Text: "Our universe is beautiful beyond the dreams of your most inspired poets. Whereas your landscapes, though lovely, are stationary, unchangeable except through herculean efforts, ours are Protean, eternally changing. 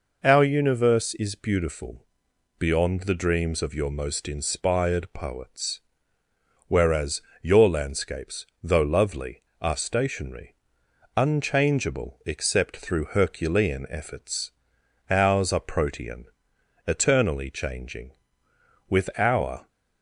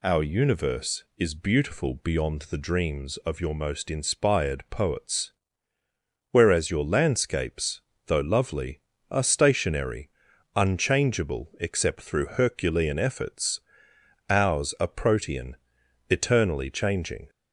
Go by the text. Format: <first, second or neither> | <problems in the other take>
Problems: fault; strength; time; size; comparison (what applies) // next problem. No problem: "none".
second | pauses between "beautiful" and "beyond"; noticeable; at 2.0 s; 0.54 s long // pauses between "Whereas" and "your"; slight; at 7.2 s; 0.22 s long // goes on to say "With our"; noticeable; from 18.8 s on; 0.78 s long